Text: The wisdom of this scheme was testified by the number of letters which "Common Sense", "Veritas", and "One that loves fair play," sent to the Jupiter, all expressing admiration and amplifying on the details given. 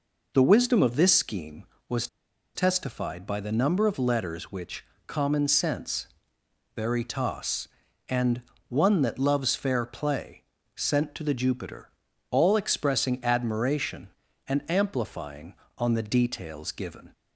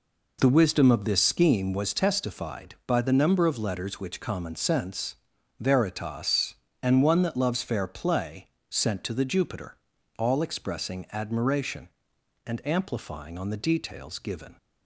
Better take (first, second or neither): second